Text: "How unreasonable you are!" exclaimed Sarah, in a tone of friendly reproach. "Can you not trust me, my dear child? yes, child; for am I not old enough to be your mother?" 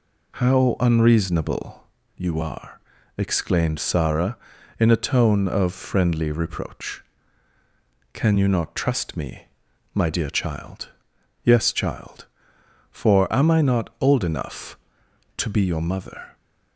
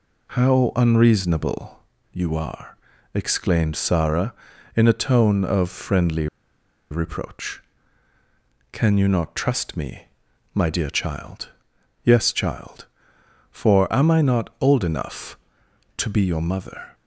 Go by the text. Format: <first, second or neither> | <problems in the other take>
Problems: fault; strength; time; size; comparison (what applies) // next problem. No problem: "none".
first | pauses between "unreasonable" and "you"; slight; at 1.7 s; 0.34 s long; slight in the first // pauses between "friendly" and "reproach"; noticeable; at 6.2 s; 0.64 s long